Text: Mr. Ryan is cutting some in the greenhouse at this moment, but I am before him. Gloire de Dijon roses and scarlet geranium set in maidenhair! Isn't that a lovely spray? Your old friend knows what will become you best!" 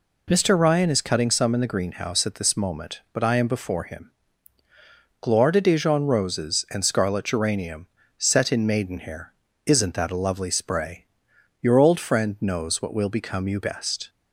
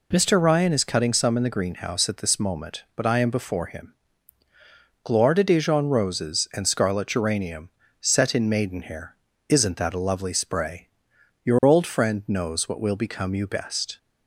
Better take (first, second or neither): neither